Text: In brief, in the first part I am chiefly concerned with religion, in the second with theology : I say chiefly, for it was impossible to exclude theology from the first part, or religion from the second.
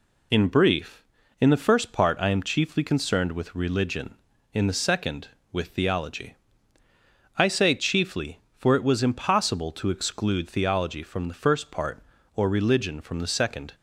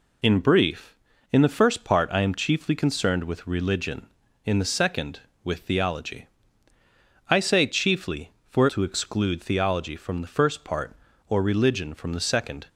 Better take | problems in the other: first | skips "it was impossible"; at 8.6 s

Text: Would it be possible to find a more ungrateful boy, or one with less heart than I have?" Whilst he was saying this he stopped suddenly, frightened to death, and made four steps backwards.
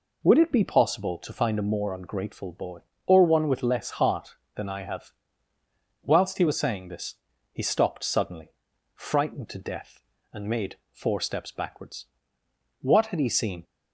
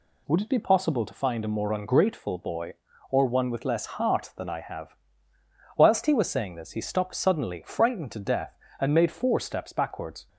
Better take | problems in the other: second | pauses between "this" and "he"; at 7.1 s; 0.38 s long // pauses between "made" and "four"; slight; at 10.7 s; 0.16 s long // goes on to say "What had he seen"; noticeable; from 12.8 s on; 0.82 s long

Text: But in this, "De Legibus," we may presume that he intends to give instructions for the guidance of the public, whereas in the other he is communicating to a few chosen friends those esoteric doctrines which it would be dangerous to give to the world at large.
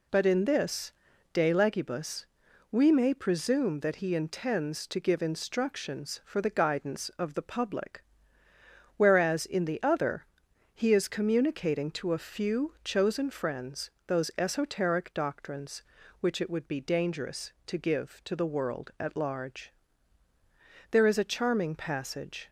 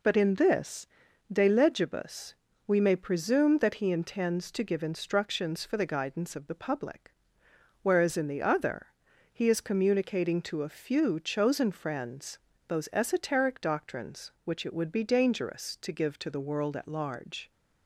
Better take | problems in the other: second | pauses between "other" and "he"; noticeable; at 10.2 s; 0.50 s long; also in the second // pauses between "friends" and "those"; slight; at 13.8 s; 0.18 s long; slight in the second // goes on to say "There is a charming passage"; from 20.9 s on; 1.5 s long

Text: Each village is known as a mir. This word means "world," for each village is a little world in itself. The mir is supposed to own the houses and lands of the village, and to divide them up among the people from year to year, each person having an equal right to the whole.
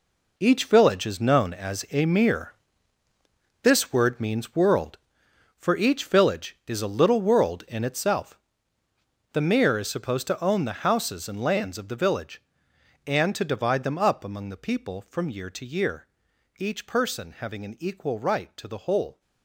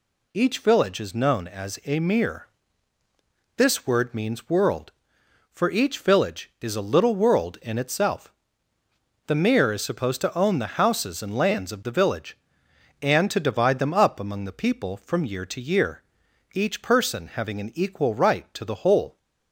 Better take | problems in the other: second | gets quieter; strong; throughout; 11.5 dB

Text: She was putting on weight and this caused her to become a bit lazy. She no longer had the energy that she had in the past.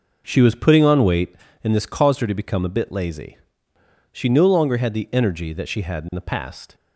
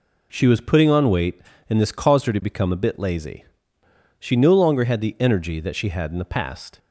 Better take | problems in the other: second | starts louder than the rest; noticeable; until 1.4 s; 5.5 dB

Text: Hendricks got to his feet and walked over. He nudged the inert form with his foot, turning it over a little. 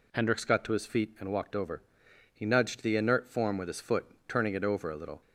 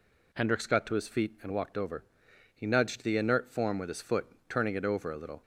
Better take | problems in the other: neither | none

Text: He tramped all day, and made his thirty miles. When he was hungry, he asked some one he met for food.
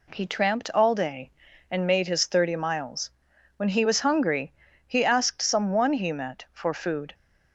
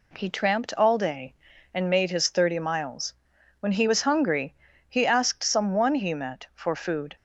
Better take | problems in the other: neither | none

